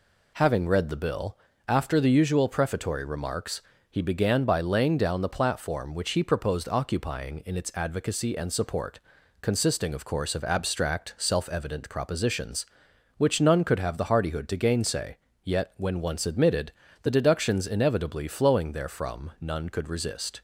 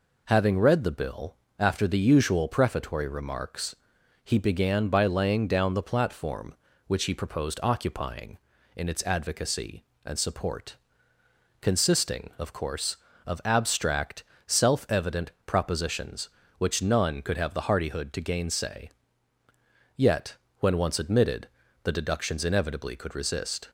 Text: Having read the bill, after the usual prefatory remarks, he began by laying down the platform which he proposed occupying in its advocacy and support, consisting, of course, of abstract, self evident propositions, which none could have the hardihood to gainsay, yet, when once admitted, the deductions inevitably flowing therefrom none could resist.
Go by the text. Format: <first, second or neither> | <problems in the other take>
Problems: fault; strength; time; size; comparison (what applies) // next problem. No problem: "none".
first | pauses between "evident" and "propositions"; slight; at 15.2 s; 0.16 s long // skips "flowing therefrom none"; at 22.9 s